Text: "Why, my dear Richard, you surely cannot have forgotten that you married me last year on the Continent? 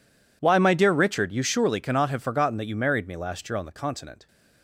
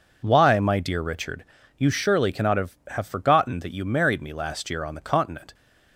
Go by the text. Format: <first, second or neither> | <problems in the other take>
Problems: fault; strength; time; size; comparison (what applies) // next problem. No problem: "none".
first | says "have" twice; at 2.9 s